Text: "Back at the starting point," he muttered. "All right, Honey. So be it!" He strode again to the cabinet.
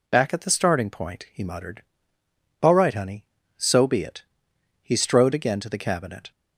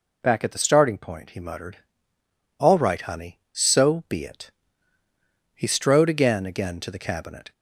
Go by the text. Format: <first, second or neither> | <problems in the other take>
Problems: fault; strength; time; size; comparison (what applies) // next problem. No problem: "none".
first | says "again" twice; at 6.4 s